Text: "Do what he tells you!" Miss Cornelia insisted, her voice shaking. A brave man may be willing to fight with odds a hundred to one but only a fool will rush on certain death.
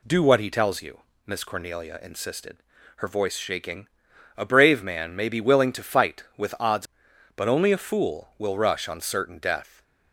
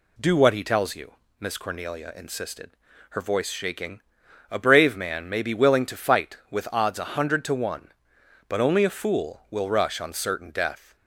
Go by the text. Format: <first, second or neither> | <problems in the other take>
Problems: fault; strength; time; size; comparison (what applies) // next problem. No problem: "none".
second | skips "a hundred to one"; at 7.1 s